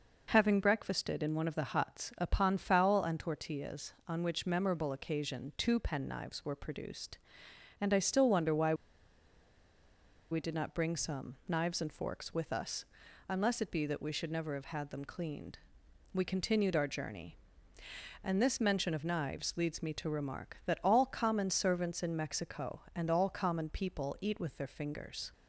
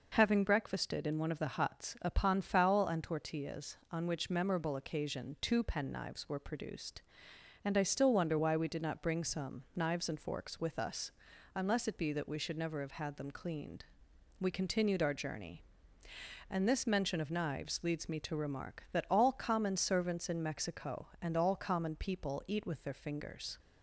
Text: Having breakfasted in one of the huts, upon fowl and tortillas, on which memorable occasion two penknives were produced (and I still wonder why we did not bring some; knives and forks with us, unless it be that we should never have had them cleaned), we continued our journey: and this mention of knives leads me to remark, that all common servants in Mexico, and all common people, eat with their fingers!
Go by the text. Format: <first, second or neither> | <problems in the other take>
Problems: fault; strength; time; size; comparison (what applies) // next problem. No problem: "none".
second | pauses between "why" and "we"; strong; at 8.7 s; 1.5 s long